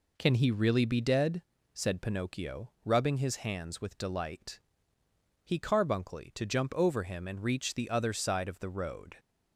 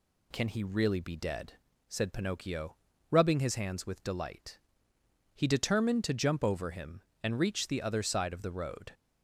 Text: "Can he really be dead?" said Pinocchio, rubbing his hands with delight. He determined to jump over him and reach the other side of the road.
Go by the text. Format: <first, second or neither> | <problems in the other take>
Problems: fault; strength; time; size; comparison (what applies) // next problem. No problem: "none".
second | says "carbuncly" for "determined"; at 5.5 s